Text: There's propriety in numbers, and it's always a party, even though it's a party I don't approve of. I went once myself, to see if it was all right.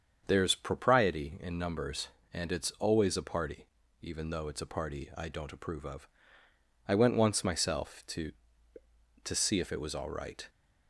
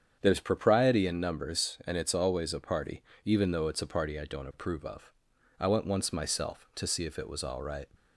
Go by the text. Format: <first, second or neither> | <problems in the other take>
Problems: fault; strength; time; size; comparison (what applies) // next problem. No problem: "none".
second | starts louder than the rest; strong; until 1.2 s; 7 dB; strong in the second // says "to" twice; at 9.2 s